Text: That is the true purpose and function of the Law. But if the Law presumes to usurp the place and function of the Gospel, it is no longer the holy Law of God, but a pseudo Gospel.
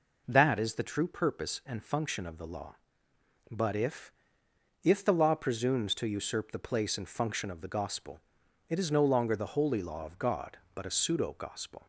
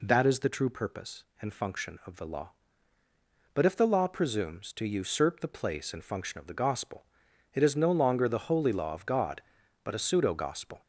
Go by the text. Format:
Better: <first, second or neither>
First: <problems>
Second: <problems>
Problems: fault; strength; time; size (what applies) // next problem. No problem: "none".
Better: second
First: says "if" twice; at 4.8 s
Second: none